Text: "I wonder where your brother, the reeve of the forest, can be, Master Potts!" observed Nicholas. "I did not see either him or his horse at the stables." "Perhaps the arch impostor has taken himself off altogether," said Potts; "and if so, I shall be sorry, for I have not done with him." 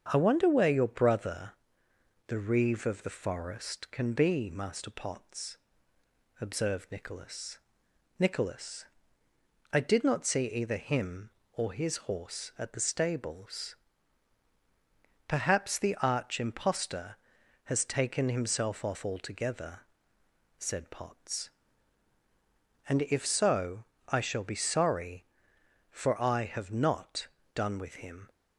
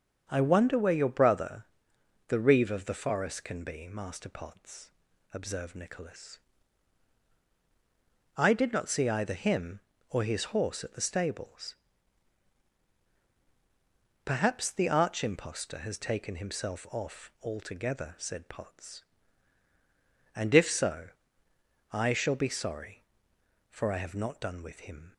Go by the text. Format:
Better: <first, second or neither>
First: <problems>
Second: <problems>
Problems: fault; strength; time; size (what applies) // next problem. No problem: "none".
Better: second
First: starts louder than the rest; strong; until 1.1 s; 7 dB // says "Nicholas" twice; at 8.1 s // pauses between "not" and "done"; slight; at 27.2 s; 0.28 s long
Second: starts louder than the rest; until 1.2 s; 7 dB